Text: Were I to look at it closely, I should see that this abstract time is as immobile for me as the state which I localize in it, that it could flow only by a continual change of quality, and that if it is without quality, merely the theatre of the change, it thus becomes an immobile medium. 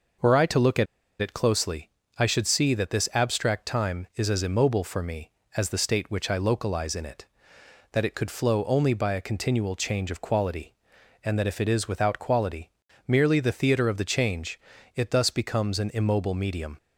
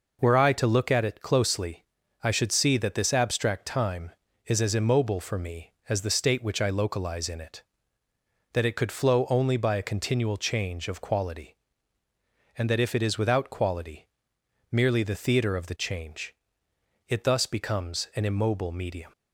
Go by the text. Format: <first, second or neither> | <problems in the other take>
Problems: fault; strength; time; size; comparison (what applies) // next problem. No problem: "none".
second | pauses between "at" and "it"; at 0.8 s; 0.36 s long